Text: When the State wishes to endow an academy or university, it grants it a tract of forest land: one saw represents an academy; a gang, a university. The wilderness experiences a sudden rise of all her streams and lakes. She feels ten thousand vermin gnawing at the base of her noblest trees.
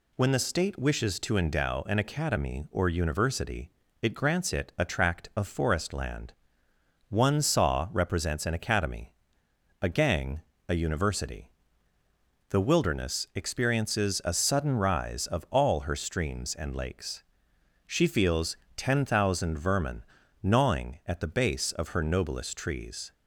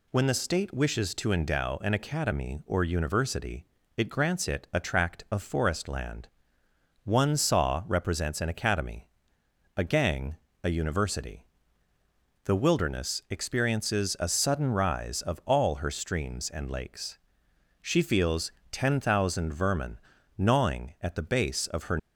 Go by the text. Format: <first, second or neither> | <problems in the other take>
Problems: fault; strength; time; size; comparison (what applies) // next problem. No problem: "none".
first | pauses between "feels" and "ten"; slight; at 18.4 s; 0.22 s long; slight in the first // pauses between "vermin" and "gnawing"; at 19.9 s; 0.40 s long; also in the first // stops before "noblest trees"; at 21.9 s